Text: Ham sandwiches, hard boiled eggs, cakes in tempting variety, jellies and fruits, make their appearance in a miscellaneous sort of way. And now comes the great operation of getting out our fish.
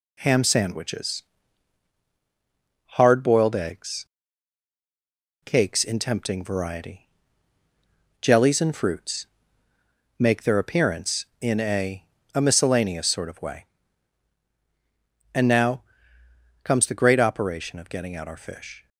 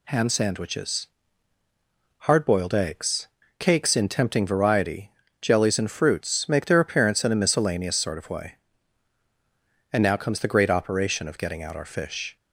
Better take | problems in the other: second | says "a" twice; at 12.3 s // pauses between "now" and "comes"; noticeable; at 15.8 s; 0.82 s long

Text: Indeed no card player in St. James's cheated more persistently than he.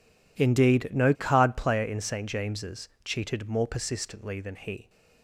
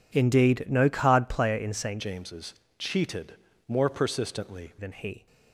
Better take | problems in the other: first | changes voice from "James's" to "persistently"; from 1.9 to 4.7 s; 2.8 s long // pauses between "James's" and "cheated"; slight; at 2.5 s; 0.24 s long; slight in the first // pauses between "cheated" and "more"; slight; at 3.3 s; 0.32 s long

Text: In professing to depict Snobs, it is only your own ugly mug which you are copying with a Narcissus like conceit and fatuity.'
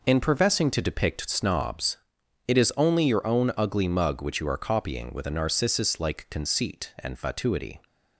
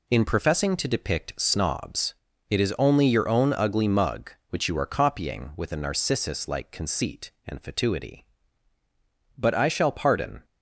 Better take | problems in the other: first | goes on to say "But I shall pardon"; noticeable; from 9.3 s on; 1.0 s long

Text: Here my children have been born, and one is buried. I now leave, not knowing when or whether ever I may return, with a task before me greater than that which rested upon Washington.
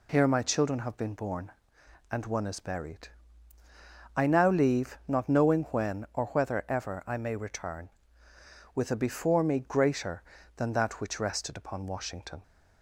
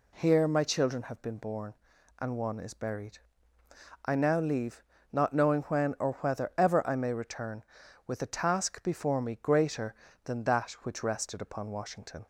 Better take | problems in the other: second | skips "task"; at 8.9 s

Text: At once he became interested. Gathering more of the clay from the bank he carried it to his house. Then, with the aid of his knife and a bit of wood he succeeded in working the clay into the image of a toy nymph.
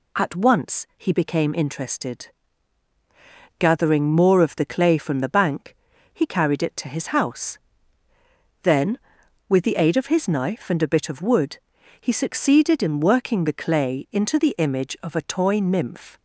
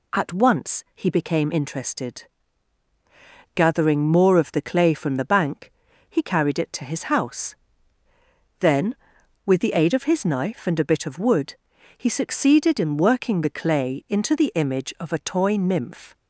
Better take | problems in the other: neither | pauses between "bank" and "he"; the same in both // pauses between "wood" and "he"; the same in both

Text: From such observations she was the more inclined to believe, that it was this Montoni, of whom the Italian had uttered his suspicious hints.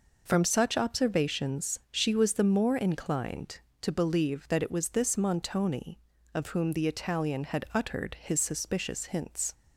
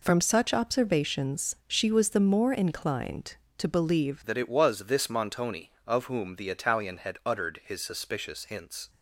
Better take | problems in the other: first | changes voice at "that"; from 4.2 s on; 4.6 s long

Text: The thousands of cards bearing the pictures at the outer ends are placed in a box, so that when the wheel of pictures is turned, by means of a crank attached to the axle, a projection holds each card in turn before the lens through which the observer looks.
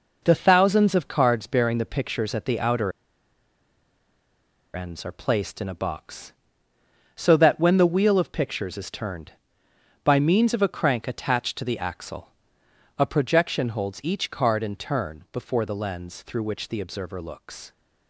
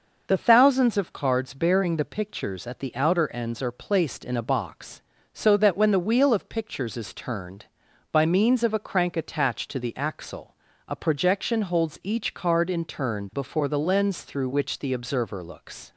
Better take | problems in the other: second | pauses between "outer" and "ends"; strong; at 2.9 s; 1.8 s long

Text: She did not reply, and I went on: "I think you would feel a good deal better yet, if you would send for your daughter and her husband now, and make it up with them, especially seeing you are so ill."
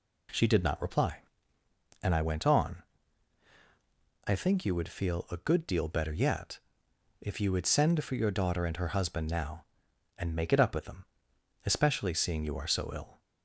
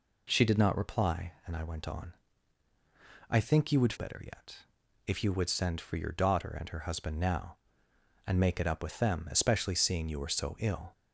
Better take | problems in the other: first | skips "feel a good deal"; at 3.9 s

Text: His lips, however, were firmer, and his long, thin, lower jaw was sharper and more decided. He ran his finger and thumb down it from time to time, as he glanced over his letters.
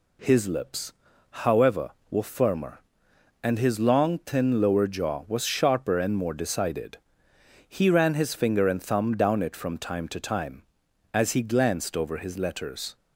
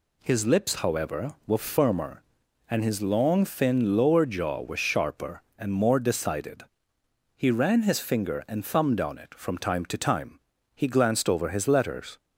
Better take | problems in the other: first | skips "as"; at 10.5 s

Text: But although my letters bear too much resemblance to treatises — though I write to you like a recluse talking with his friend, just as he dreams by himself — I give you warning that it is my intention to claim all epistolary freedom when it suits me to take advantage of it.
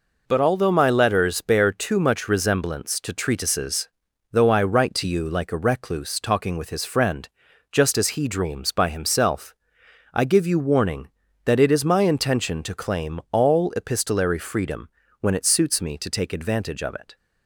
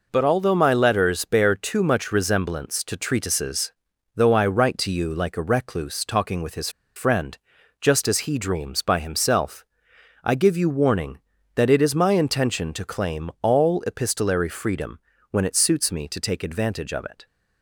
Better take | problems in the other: first | pauses between "his" and "friend"; slight; at 6.6 s; 0.27 s long // pauses between "freedom" and "when"; slight; at 14.9 s; 0.32 s long; slight in the first

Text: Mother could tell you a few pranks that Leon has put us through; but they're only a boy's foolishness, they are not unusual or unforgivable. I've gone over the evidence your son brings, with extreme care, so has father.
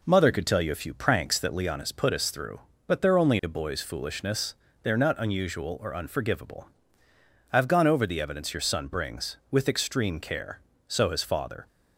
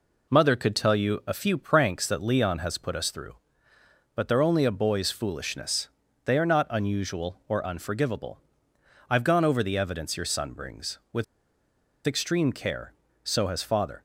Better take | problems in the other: first | pauses between "with" and "extreme"; noticeable; at 11.2 s; 0.82 s long

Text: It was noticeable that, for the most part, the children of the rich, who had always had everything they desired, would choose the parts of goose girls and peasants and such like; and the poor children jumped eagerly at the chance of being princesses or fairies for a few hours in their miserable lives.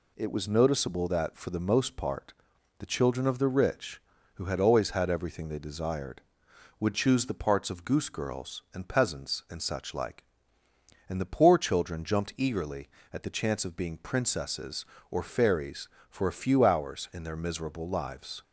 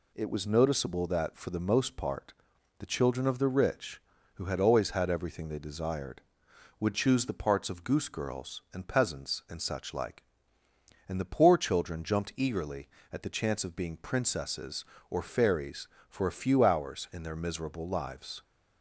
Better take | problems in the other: neither | none

